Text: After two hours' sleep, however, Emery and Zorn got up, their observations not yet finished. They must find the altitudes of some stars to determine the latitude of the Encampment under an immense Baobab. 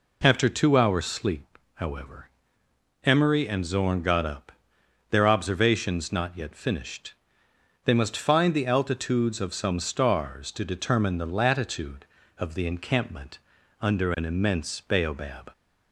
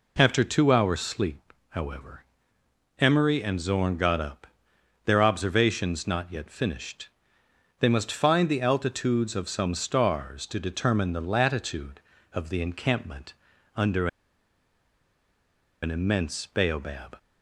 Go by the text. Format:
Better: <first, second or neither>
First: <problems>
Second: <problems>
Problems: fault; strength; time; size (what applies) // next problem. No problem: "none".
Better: first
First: pauses between "Encampment" and "under"; at 13.4 s; 0.40 s long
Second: pauses between "Encampment" and "under"; at 13.3 s; 0.40 s long // pauses between "under" and "an"; strong; at 14.0 s; 1.7 s long